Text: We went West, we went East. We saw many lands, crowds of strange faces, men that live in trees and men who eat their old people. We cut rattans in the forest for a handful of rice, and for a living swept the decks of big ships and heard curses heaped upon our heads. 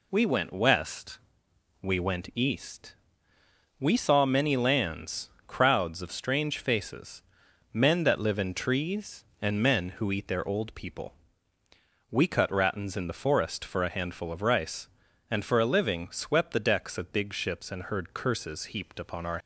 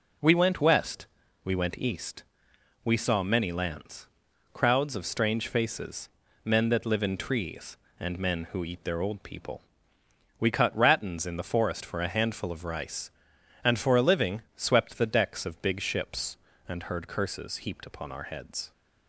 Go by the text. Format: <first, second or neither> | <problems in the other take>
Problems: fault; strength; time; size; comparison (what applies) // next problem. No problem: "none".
second | stops before "heads"; at 19.3 s